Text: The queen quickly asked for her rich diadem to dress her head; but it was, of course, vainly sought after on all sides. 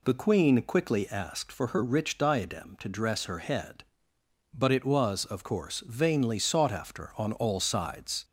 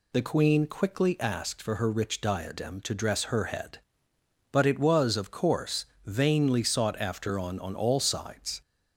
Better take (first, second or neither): first